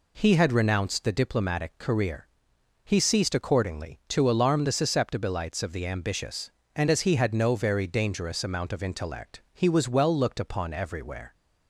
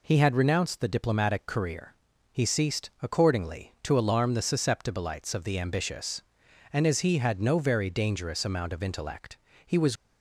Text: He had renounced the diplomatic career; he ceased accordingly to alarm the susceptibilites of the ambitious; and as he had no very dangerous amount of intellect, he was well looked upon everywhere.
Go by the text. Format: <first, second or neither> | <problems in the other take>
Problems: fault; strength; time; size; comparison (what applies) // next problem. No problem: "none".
first | stops before "well looked upon everywhere"; at 9.9 s